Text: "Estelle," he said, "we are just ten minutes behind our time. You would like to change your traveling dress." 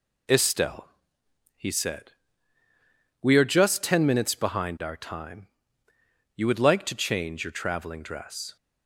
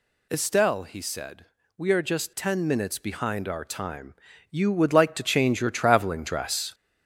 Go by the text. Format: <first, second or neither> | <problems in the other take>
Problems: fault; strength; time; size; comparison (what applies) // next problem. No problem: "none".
first | gets louder; noticeable; throughout; 5 dB